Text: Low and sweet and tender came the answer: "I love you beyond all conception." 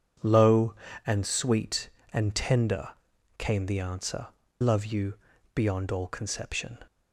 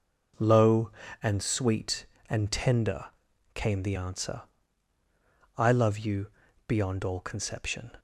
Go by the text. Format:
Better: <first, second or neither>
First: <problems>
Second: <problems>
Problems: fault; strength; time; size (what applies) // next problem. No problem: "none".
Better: second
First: pauses between "tender" and "came"; noticeable; at 2.8 s; 0.50 s long // skips "I"; at 4.4 s // pauses between "you" and "beyond"; slight; at 5.1 s; 0.36 s long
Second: pauses between "tender" and "came"; noticeable; at 3.0 s; 0.50 s long // pauses between "you" and "beyond"; slight; at 6.3 s; 0.36 s long